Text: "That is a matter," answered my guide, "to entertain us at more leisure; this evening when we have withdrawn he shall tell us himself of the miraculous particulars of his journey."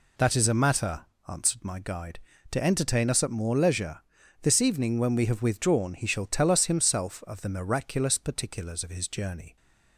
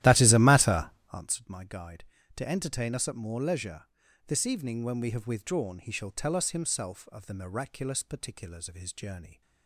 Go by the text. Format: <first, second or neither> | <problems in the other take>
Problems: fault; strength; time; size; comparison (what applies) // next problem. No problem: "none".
first | starts louder than the rest; strong; until 1.2 s; 14 dB